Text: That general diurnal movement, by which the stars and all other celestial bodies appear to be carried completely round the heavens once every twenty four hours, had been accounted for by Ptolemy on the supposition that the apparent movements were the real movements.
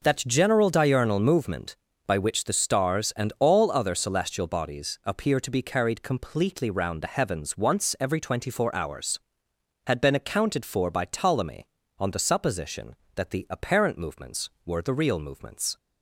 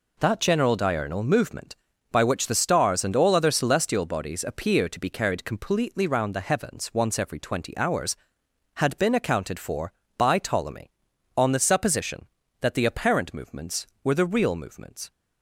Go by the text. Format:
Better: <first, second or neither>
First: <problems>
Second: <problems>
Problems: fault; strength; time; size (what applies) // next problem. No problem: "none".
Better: first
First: none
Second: skips "four"; at 7.7 s